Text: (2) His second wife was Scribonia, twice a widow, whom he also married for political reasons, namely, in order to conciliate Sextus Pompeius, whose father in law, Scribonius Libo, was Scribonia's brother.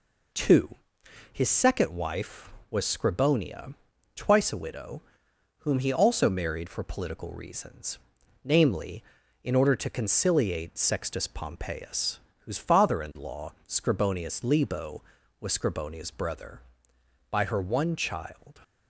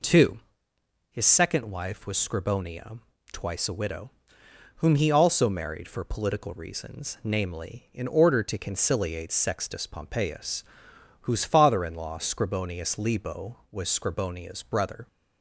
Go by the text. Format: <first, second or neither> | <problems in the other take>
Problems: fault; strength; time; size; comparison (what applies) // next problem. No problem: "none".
second | goes on to say "By her one child"; noticeable; from 17.3 s on; 1.3 s long